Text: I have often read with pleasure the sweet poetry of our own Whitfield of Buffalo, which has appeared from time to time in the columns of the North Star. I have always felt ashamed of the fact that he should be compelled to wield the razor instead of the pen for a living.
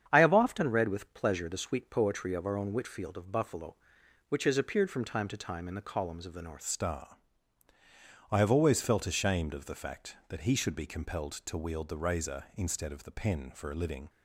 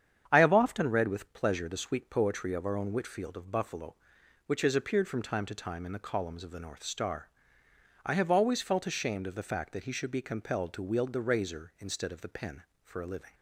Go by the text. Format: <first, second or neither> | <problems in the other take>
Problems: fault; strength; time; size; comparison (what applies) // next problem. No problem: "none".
second | starts louder than the rest; strong; until 1.1 s; 8 dB; strong in the second // changes voice at "Star"; from 6.6 s on; 7.4 s long